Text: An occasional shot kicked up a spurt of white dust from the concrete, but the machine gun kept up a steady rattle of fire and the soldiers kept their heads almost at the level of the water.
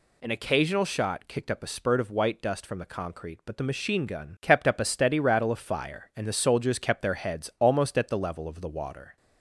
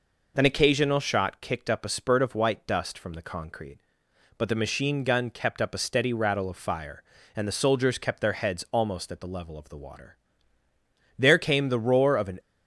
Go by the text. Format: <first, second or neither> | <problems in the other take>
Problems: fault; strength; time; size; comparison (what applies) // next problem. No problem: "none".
first | goes on to say "There came the roar of an"; noticeable; from 11.1 s on; 1.2 s long